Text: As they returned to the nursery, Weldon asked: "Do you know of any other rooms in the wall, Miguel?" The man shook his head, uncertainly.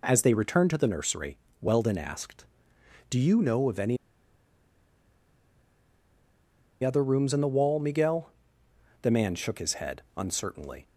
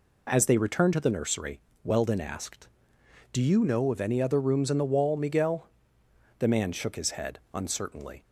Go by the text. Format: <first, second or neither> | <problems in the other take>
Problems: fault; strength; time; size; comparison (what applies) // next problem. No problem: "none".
second | pauses between "any" and "other"; strong; at 3.9 s; 2.8 s long